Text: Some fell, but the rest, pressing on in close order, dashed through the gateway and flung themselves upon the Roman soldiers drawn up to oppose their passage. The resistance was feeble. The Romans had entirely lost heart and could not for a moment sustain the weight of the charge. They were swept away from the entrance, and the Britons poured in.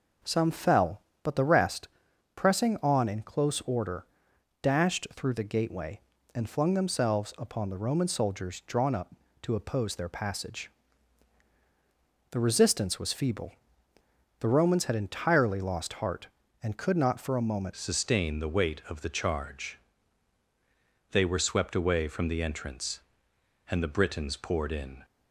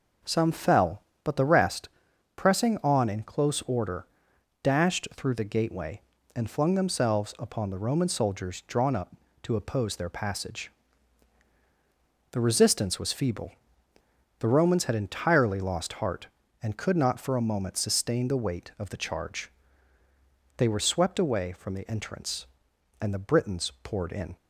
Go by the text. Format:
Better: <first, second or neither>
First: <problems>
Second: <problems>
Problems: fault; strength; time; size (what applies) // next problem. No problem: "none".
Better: second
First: changes voice at "sustain"; from 17.7 s on; 7.3 s long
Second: none